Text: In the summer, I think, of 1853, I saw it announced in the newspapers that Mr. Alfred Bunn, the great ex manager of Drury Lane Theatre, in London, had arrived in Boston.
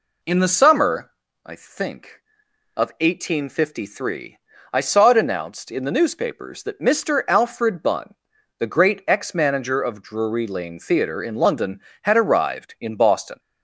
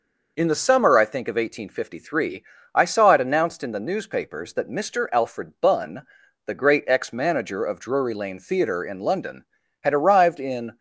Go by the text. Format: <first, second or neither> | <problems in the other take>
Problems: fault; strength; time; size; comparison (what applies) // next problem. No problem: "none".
first | stops before "Boston"; at 10.7 s